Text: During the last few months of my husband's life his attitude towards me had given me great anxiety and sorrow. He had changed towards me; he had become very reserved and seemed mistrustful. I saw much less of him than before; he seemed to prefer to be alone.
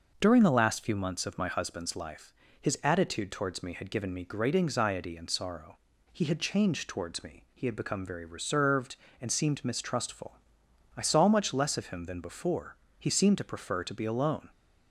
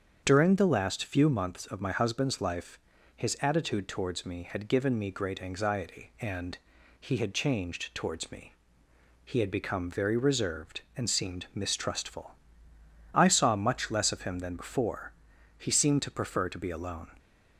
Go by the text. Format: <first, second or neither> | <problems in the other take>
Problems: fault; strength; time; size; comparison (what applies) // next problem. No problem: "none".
first | starts louder than the rest; strong; until 1.2 s; 7.5 dB // pauses between "life" and "his"; slight; at 2.7 s; 0.36 s long; slight in the first // skips "sorrow"; at 6.7 s